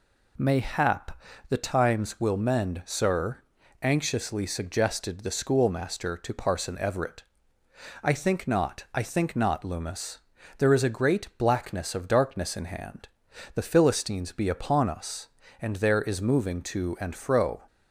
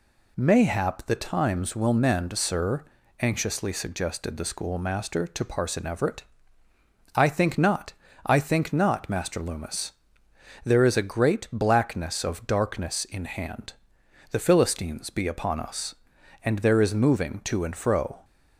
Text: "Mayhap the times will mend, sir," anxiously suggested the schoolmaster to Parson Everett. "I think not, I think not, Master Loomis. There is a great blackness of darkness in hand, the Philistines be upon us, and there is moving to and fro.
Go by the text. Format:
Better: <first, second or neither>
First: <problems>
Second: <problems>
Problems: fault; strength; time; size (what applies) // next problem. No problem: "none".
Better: second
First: pauses between "Mayhap" and "the"; slight; at 1.1 s; 0.30 s long // skips "Master"; at 9.6 s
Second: none